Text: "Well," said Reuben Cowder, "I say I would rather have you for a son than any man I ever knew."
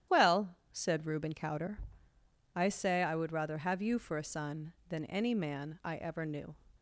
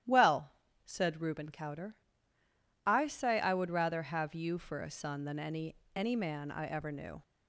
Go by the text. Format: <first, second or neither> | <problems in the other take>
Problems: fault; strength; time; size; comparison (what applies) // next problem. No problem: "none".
first | starts louder than the rest; strong; until 1.4 s; 12 dB; strong in the first // says "any" twice; at 5.9 s